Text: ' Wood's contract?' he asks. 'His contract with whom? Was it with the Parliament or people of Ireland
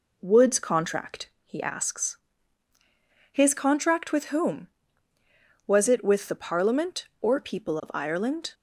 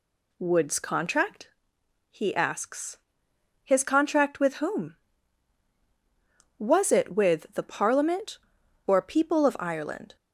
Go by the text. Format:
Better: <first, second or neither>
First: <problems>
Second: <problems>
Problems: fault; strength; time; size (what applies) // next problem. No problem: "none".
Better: neither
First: none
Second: none